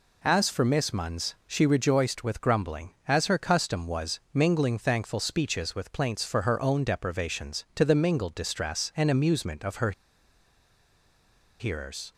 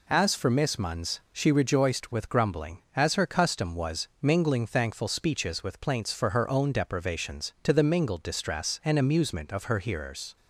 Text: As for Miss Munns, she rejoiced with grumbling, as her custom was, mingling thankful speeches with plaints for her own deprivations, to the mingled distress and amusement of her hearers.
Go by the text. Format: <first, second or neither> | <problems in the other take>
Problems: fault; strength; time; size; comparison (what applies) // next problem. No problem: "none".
second | pauses between "her" and "hearers"; strong; at 9.9 s; 1.6 s long